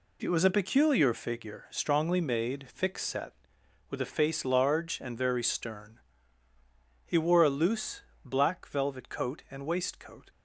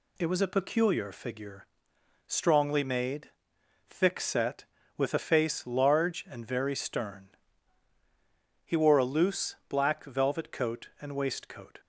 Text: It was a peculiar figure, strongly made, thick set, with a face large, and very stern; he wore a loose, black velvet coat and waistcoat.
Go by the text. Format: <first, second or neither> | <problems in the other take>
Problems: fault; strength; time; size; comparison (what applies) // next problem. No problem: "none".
neither | none